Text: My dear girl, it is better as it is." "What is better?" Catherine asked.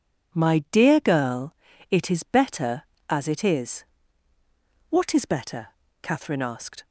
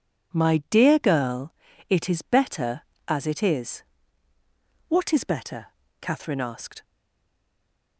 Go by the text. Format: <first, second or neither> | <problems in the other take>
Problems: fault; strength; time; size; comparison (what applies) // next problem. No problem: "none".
first | stays silent after the last word; noticeable; from 6.8 s on; 1.1 s long